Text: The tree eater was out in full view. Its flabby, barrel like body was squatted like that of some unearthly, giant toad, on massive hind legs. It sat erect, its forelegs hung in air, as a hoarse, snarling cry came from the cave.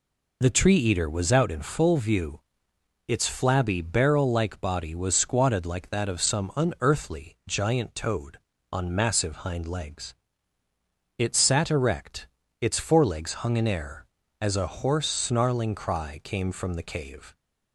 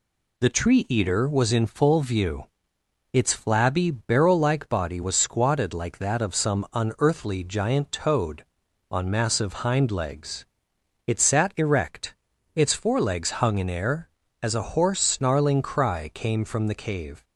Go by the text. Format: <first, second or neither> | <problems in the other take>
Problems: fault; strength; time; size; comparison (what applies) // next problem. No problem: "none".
first | skips "out"; at 1.5 s